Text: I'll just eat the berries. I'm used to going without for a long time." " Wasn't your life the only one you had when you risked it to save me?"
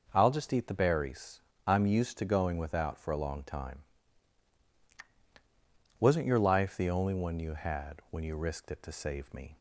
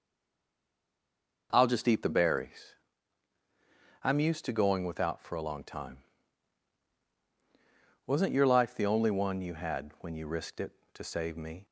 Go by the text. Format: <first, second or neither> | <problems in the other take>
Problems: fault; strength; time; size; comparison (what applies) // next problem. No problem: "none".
first | stays silent before the first word; noticeable; until 1.5 s; 1.5 s long // starts louder than the rest; until 2.5 s; 6.5 dB; also in the first